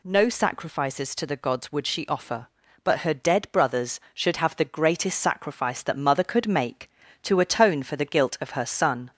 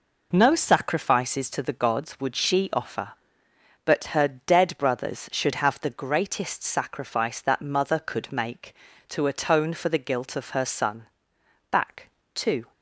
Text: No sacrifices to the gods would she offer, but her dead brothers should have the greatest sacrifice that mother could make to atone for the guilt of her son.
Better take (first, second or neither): first